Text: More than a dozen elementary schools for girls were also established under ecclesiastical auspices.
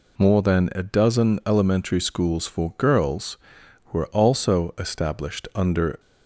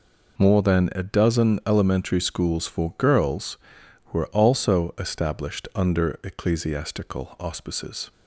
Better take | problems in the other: second | stops before "ecclesiastical auspices"; at 5.9 s

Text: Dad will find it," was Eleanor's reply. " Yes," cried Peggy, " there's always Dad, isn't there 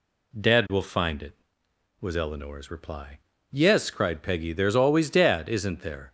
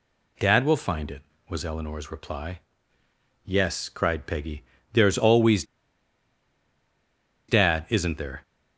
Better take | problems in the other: first | pauses between "always" and "Dad"; strong; at 5.6 s; 1.8 s long

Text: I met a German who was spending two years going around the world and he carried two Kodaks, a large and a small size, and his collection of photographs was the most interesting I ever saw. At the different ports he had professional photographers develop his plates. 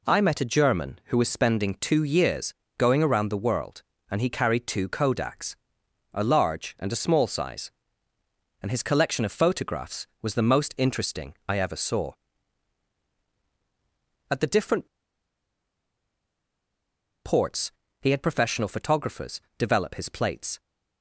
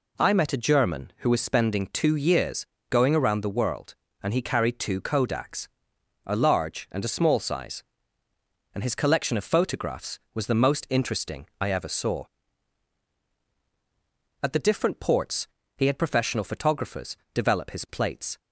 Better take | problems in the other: second | pauses between "years" and "going"; slight; at 2.5 s; 0.24 s long; slight in the second // pauses between "different" and "ports"; strong; at 14.8 s; 2.3 s long // pauses between "ports" and "he"; slight; at 17.7 s; 0.28 s long; slight in the second // pauses between "photographers" and "develop"; slight; at 19.4 s; 0.16 s long; slight in the second

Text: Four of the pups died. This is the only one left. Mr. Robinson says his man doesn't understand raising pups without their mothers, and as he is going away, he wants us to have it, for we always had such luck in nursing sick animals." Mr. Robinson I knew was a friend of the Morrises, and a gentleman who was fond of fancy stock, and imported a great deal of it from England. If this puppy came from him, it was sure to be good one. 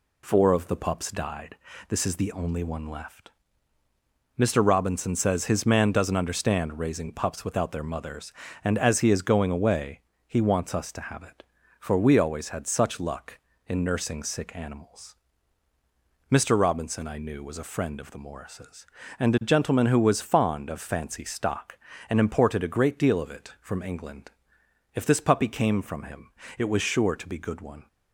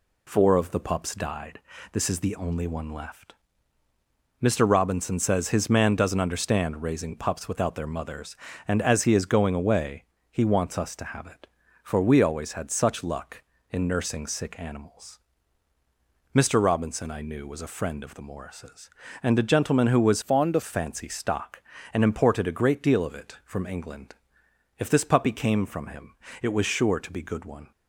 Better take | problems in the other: first | changes voice from "fond" to "of"; from 20.2 to 20.6 s; 0.4 s long

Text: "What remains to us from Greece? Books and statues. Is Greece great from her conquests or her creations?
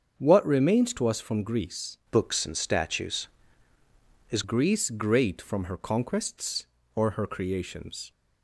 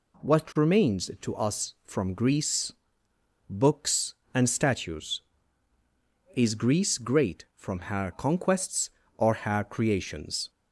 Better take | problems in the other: second | starts louder than the rest; until 1.1 s; 7 dB // changes voice from "Books" to "Is"; from 2.1 to 4.4 s; 2.3 s long

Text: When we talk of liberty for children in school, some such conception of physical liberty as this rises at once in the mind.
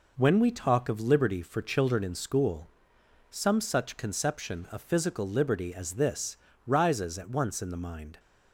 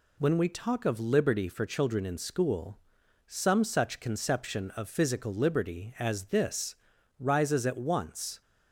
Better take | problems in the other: first | pauses between "this" and "rises"; noticeable; at 6.7 s; 0.46 s long; slight in the first // stops before "in the mind"; at 8.4 s

